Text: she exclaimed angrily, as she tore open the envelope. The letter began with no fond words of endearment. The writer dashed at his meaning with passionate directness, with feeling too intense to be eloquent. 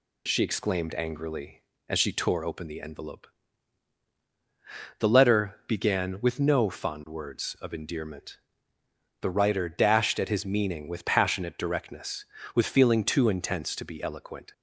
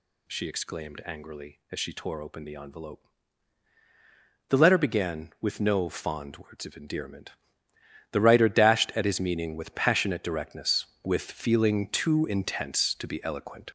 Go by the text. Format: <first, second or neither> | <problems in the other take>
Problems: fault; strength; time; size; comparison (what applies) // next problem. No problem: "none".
first | gets louder; throughout; 6.5 dB